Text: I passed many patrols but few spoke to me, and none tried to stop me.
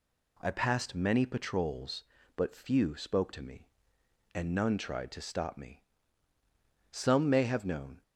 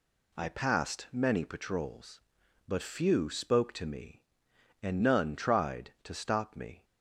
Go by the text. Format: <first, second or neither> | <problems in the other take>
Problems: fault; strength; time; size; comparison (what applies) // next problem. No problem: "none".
second | goes on to say "Some may have known"; noticeable; from 6.9 s on; 1.1 s long